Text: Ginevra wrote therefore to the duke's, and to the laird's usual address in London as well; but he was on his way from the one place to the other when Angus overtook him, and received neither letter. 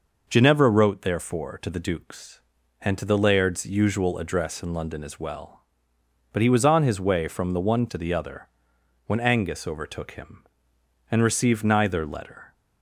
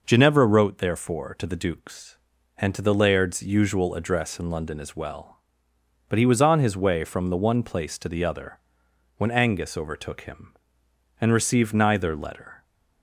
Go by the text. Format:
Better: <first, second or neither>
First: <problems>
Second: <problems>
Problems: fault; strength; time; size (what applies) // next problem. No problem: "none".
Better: second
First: skips "place"; at 7.8 s // pauses between "other" and "when"; noticeable; at 8.4 s; 0.58 s long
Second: pauses between "other" and "when"; noticeable; at 8.5 s; 0.58 s long